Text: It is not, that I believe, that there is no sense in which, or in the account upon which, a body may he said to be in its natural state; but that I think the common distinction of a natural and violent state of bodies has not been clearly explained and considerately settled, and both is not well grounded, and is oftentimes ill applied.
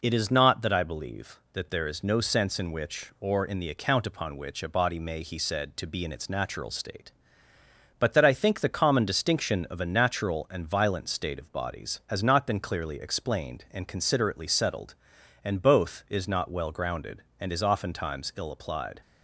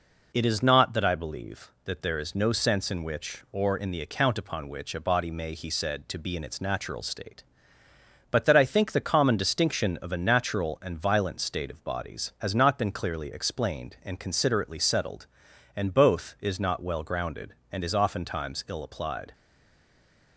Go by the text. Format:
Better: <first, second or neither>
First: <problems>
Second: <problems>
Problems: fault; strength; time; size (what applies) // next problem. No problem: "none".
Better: first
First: none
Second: stays silent after the last word; from 19.3 s on; 1.0 s long